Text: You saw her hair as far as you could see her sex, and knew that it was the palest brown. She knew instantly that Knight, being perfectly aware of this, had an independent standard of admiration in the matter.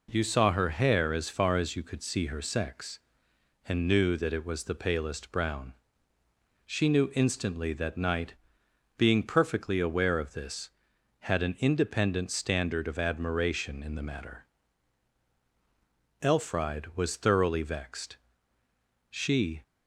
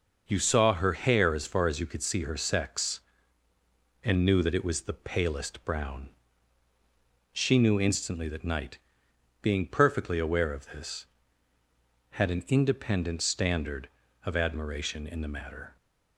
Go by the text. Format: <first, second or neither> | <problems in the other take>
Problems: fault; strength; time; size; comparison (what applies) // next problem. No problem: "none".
second | goes on to say "Elfride was thoroughly vexed She"; strong; from 16.2 s on; 3.3 s long